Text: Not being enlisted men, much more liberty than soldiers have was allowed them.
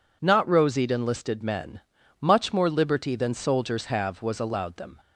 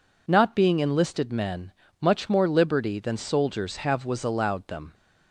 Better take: second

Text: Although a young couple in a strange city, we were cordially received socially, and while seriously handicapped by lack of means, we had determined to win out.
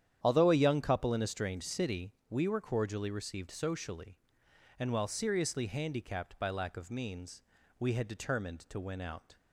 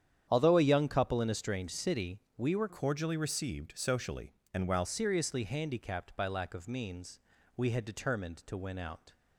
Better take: first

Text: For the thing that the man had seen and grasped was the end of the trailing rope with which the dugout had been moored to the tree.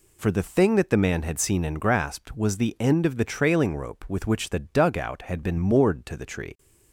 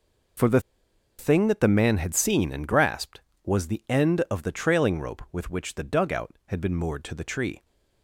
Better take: first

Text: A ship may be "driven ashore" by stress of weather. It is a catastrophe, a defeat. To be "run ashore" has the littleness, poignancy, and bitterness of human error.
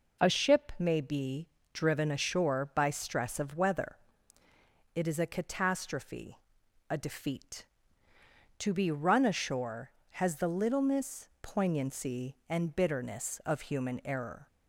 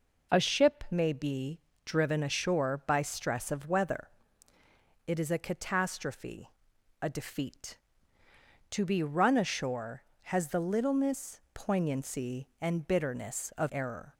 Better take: first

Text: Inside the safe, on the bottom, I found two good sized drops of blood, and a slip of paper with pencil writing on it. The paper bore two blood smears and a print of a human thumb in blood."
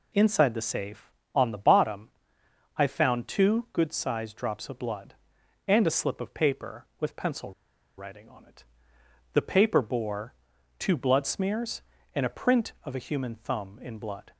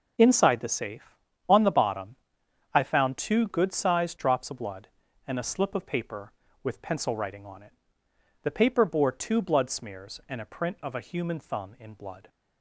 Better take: second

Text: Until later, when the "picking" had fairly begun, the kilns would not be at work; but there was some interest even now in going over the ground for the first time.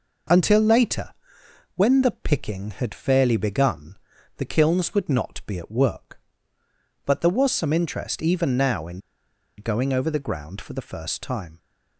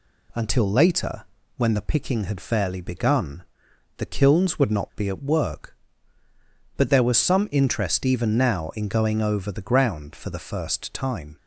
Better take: second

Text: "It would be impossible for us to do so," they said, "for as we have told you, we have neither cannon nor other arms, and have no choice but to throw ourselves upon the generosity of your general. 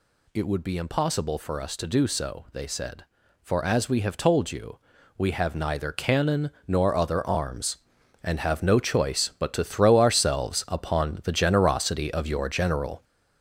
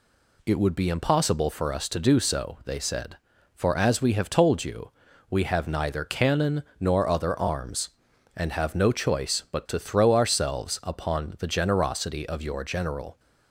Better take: second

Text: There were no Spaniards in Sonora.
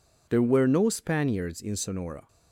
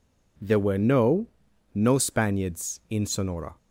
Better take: first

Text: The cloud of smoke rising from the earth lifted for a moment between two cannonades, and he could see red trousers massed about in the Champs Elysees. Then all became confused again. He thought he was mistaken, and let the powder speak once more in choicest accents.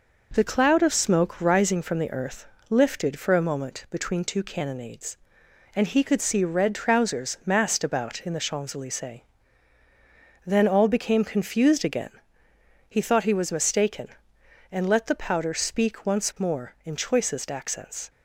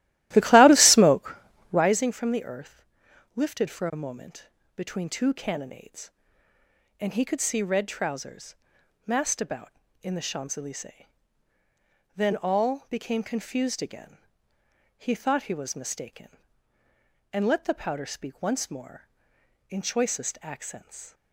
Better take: first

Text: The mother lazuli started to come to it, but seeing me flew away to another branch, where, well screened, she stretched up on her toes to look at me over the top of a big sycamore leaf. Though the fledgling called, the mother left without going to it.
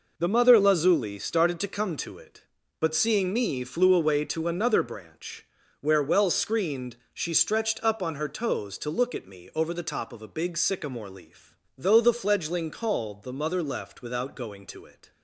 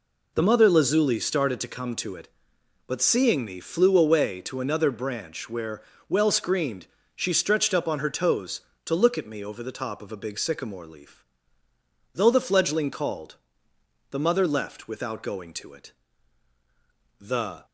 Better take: first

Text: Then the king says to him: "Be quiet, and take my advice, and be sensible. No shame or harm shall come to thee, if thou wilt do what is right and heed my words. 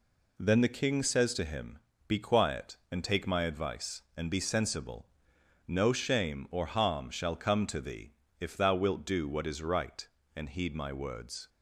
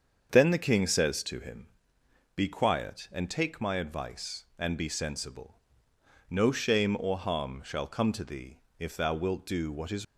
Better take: first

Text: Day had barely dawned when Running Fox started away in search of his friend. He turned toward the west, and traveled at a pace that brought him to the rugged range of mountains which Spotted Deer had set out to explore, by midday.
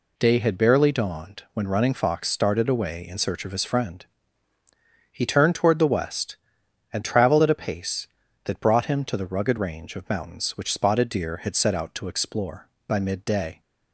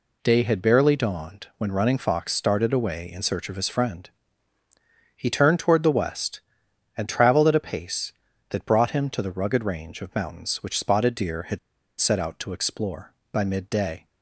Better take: first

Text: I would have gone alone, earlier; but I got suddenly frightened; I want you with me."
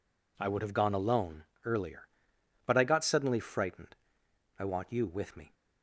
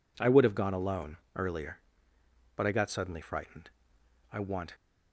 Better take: first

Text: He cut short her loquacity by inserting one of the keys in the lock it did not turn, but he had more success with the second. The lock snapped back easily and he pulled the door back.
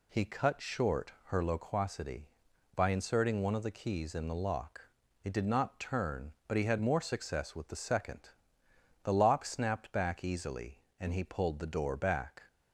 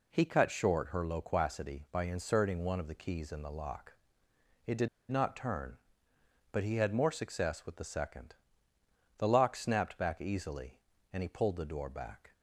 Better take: first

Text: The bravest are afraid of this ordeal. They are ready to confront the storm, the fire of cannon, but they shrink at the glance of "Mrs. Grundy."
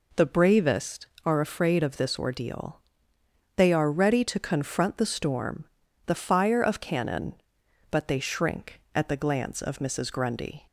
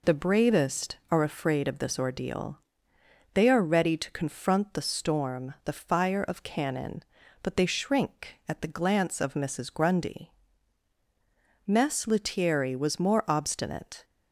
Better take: first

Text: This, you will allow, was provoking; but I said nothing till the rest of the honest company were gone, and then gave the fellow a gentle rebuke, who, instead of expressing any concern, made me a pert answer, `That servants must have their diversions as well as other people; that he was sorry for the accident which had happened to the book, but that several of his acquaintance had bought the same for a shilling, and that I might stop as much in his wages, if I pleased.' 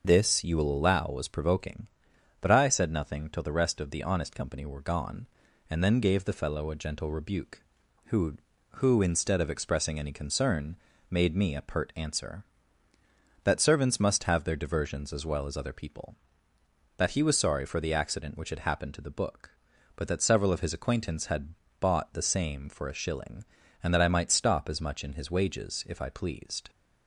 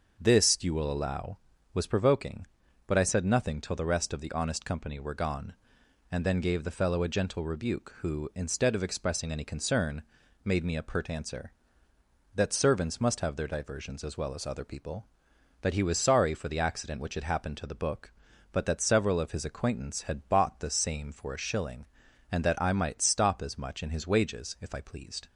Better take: second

